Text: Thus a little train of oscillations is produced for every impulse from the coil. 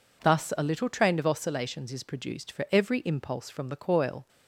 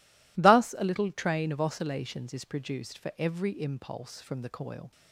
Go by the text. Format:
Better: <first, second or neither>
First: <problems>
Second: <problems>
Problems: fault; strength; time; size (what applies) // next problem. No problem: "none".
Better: neither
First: none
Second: none